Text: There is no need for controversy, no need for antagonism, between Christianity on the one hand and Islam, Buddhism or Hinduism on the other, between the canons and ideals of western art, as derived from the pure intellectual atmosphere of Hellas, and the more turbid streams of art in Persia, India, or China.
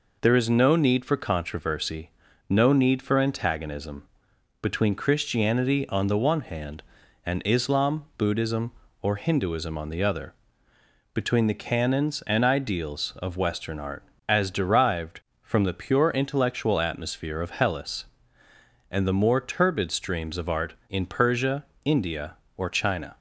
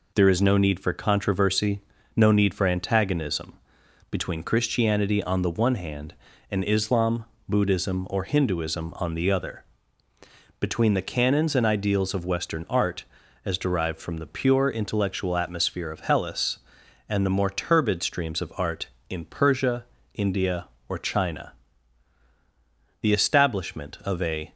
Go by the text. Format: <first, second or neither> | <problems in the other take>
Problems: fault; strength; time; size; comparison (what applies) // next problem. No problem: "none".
first | goes on to say "The establishment of a"; from 23.0 s on; 1.5 s long